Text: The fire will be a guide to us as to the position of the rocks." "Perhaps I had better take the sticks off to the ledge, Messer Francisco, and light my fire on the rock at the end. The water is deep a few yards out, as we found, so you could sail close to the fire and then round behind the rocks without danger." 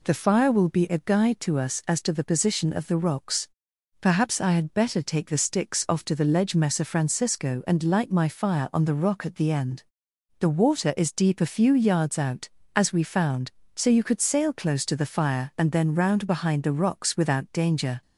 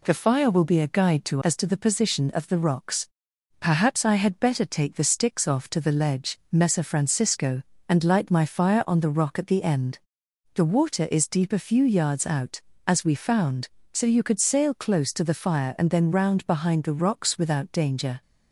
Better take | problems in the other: first | skips "us"; at 1.4 s

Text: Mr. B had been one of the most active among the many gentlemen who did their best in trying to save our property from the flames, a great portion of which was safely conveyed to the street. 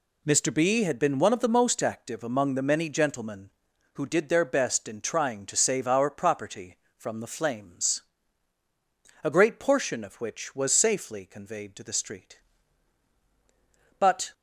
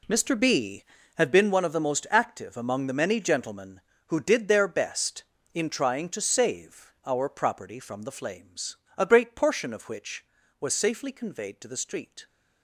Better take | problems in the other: second | goes on to say "But"; slight; from 13.9 s on; 0.34 s long

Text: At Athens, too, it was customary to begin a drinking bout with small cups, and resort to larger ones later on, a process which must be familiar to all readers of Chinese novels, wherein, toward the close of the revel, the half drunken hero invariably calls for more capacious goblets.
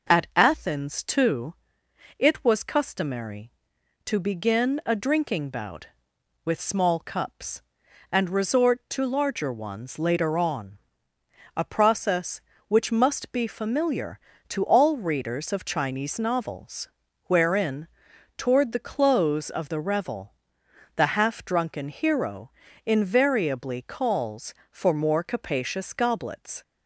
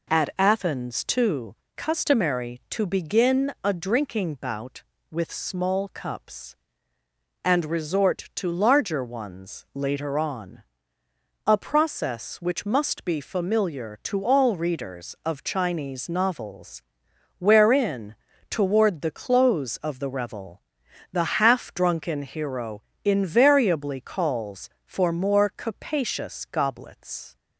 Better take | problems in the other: first | skips "it was"; at 1.6 s // pauses between "hero" and "invariably"; slight; at 22.8 s; 0.22 s long; slight in the first

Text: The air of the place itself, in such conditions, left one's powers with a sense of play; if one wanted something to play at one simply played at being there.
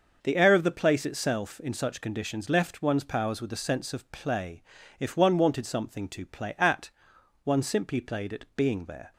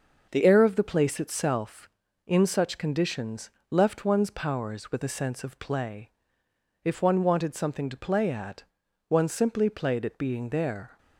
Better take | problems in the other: first | starts louder than the rest; noticeable; until 1.3 s; 6 dB; also in the first // changes voice at "air"; from 0.4 s on; 10.5 s long // pauses between "at" and "one"; at 8.6 s; 0.44 s long; noticeable in the first

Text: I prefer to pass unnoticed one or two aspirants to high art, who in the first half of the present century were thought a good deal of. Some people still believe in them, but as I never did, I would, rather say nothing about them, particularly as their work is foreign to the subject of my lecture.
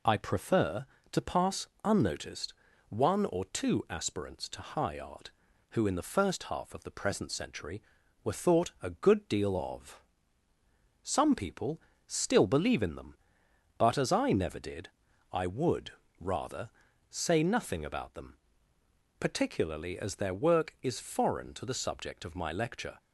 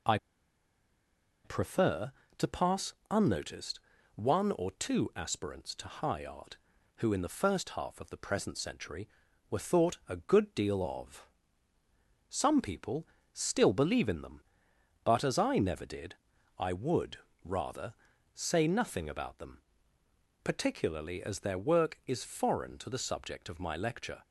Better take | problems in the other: first | pauses between "I" and "prefer"; strong; at 0.1 s; 1.2 s long // pauses between "pass" and "unnoticed"; slight; at 2.9 s; 0.18 s long; slight in the first // pauses between "unnoticed" and "one"; slight; at 3.8 s; 0.34 s long; slight in the first // pauses between "people" and "still"; slight; at 13.0 s; 0.26 s long; slight in the first // pauses between "rather" and "say"; at 17.9 s; 0.44 s long; also in the first

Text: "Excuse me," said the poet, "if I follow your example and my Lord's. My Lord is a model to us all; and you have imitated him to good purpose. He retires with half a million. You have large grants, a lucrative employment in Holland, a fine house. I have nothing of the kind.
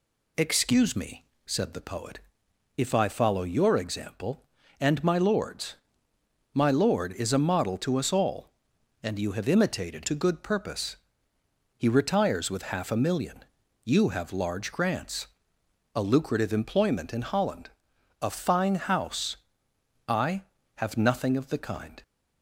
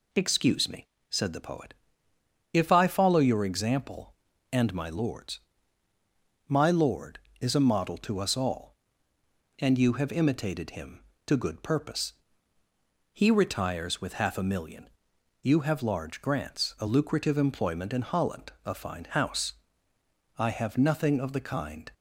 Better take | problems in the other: second | skips "him"; at 10.0 s

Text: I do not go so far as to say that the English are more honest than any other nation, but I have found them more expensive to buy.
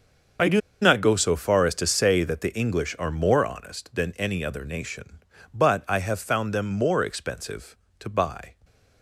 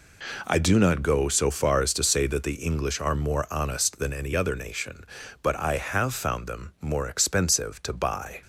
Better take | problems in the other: second | starts louder than the rest; until 1.6 s; 6.5 dB // pauses between "do" and "not"; slight; at 0.5 s; 0.22 s long

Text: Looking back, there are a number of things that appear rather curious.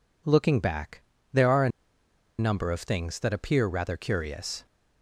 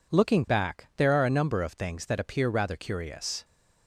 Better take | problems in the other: second | pauses between "a" and "number"; noticeable; at 1.6 s; 0.69 s long

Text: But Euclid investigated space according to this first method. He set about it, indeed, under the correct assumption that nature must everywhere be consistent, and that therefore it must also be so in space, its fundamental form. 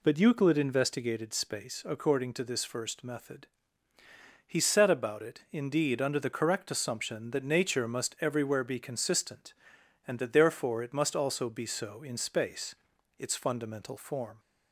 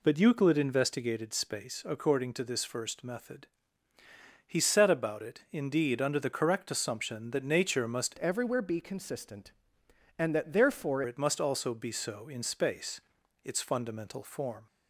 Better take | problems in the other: first | changes voice from "everywhere" to "therefore"; from 8.1 to 11.0 s; 2.9 s long

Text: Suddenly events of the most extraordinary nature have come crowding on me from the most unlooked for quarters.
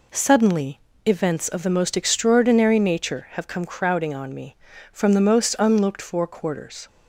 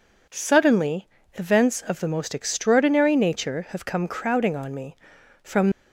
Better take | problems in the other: first | pauses between "Suddenly" and "events"; slight; at 1.0 s; 0.26 s long; slight in the first // stops before "the most unlooked for quarters"; at 5.7 s

